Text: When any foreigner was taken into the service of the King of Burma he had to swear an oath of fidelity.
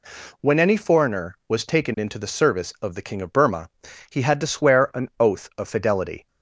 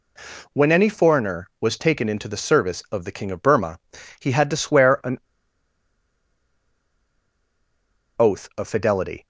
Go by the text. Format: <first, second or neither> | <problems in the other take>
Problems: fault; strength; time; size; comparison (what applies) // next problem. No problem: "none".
first | pauses between "Burma" and "he"; at 3.8 s; 0.40 s long; also in the first // pauses between "an" and "oath"; strong; at 5.1 s; 2.9 s long